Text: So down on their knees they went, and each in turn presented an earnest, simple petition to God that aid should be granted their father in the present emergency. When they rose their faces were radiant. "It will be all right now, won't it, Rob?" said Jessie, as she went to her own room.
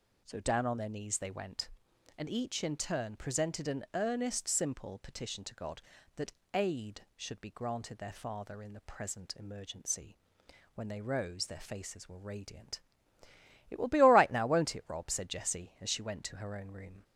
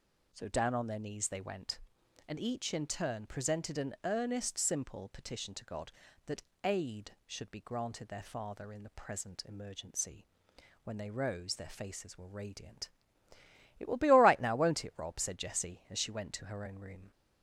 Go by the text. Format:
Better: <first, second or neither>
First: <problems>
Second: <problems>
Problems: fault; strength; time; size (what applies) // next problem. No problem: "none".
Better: neither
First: pauses between "that" and "aid"; slight; at 6.3 s; 0.22 s long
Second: pauses between "that" and "aid"; slight; at 6.4 s; 0.22 s long